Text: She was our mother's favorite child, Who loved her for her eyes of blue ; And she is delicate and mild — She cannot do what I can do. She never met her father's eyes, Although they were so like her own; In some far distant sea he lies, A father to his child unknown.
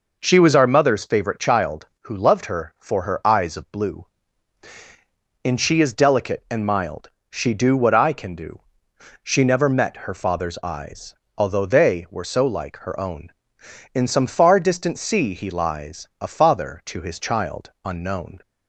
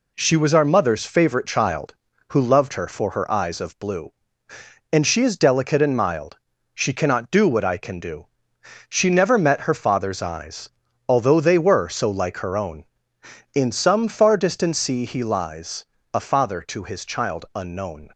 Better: second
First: skips "cannot"; at 7.5 s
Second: none

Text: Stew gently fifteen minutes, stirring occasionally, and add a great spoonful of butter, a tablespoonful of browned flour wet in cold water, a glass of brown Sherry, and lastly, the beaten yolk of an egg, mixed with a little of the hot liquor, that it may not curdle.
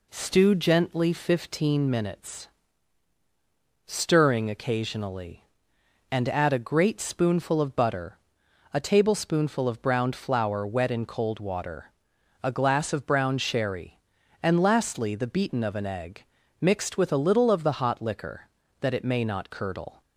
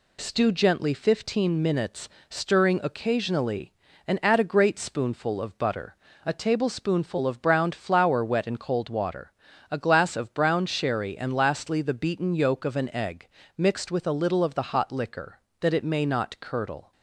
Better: second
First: skips "yolk"; at 15.6 s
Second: none

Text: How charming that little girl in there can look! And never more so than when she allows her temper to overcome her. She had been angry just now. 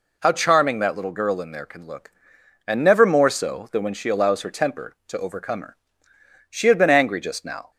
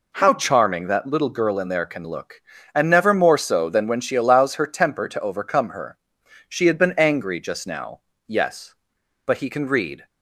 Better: first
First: none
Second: goes on to say "Yes But he can read"; strong; from 8.2 s on; 1.8 s long

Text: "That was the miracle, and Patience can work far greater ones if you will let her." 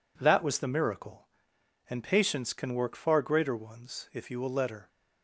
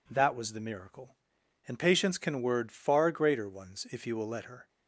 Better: first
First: none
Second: says "word" for "work"; at 2.3 s

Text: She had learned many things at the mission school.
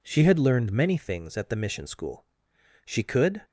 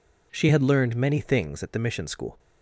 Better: second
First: goes on to say "She could"; from 2.8 s on; 0.56 s long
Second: none

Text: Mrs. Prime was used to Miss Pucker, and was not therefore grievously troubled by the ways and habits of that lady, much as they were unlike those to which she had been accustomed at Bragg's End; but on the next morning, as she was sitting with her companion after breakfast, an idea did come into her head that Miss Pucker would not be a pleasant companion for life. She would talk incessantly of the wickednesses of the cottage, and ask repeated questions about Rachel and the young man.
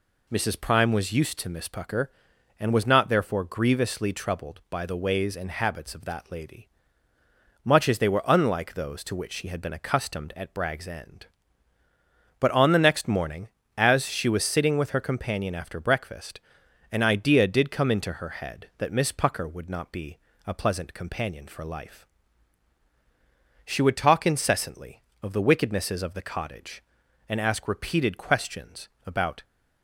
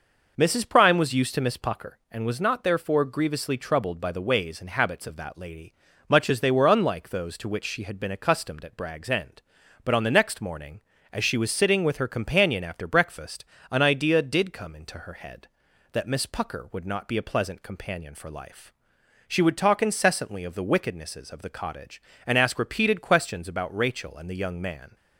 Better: second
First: pauses between "be" and "a"; slight; at 20.1 s; 0.30 s long // pauses between "questions" and "about"; slight; at 28.8 s; 0.18 s long // stops before "Rachel and the young man"; at 29.4 s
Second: none

